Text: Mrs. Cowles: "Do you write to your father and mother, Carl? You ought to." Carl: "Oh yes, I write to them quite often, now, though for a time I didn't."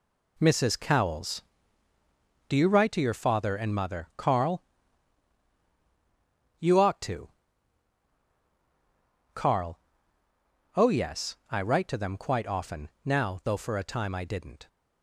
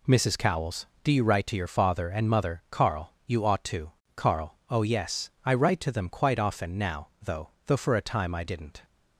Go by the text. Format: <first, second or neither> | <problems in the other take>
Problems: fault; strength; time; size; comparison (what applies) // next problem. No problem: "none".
first | says "though" twice; at 7.6 s